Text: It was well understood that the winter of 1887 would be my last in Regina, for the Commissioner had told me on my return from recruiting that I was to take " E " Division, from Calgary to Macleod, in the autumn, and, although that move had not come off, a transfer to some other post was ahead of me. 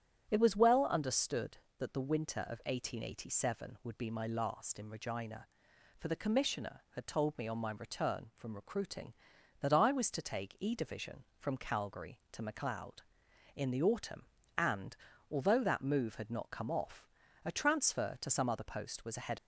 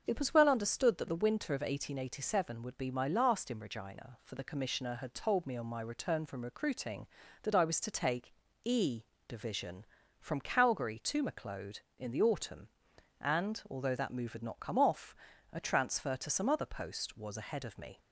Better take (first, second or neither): second